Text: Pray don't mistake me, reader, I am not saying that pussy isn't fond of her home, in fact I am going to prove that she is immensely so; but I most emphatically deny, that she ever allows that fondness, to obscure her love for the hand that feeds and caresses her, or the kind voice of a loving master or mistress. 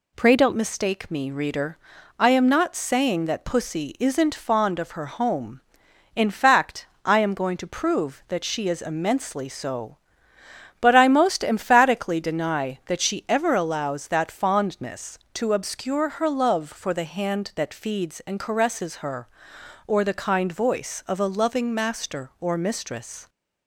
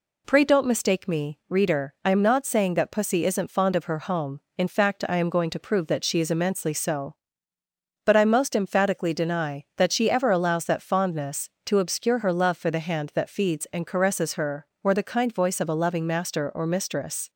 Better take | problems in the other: second | changes voice at "mistake"; from 0.5 s on; 22.7 s long // pauses between "fact" and "I"; slight; at 6.8 s; 0.18 s long

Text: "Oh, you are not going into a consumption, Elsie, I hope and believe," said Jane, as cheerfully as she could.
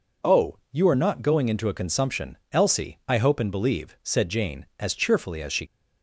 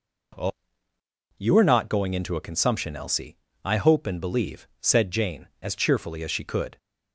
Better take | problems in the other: second | stops before "could"; at 5.6 s

